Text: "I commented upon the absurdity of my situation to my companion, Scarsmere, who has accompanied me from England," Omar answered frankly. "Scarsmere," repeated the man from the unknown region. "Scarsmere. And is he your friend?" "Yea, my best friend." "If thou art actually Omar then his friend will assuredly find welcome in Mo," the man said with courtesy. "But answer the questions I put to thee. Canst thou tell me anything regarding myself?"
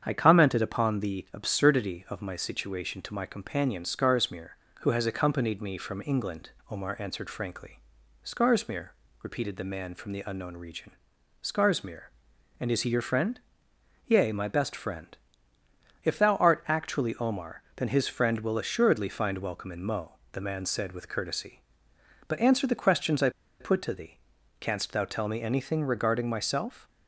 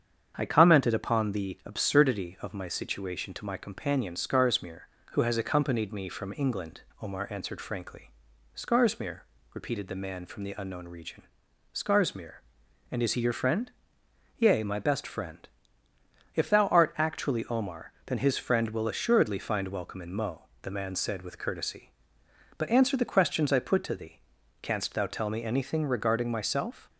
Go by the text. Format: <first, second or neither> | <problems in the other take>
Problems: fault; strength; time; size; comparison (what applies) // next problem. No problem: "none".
second | starts louder than the rest; strong; until 1.0 s; 8 dB; strong in the second // pauses between "Omar" and "then"; slight; at 17.6 s; 0.16 s long; slight in the second // pauses between "I" and "put"; slight; at 23.2 s; 0.30 s long